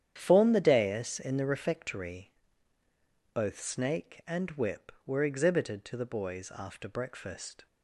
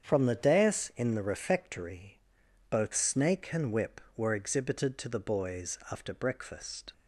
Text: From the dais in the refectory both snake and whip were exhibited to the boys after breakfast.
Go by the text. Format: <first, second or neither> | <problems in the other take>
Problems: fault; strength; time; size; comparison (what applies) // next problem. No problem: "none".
second | starts louder than the rest; strong; until 1.1 s; 9.5 dB; strong in the second // says "Form" for "From"; at 0.1 s // pauses between "refectory" and "both"; at 2.3 s; 1.0 s long; noticeable in the second